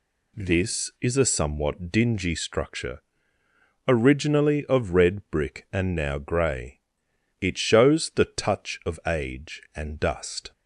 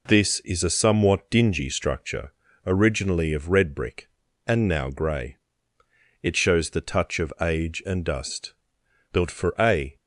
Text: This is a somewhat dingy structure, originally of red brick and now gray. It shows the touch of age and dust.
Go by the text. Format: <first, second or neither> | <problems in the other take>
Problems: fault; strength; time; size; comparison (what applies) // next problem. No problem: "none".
first | goes on to say "Built for a"; noticeable; from 9.1 s on; 0.84 s long